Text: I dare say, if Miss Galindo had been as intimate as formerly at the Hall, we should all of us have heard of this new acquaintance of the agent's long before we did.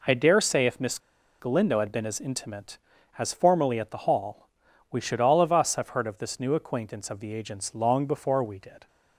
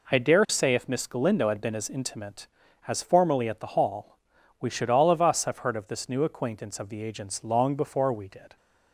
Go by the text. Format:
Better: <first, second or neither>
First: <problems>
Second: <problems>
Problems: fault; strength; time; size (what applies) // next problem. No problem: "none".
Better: second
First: pauses between "Miss" and "Galindo"; at 0.9 s; 0.41 s long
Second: none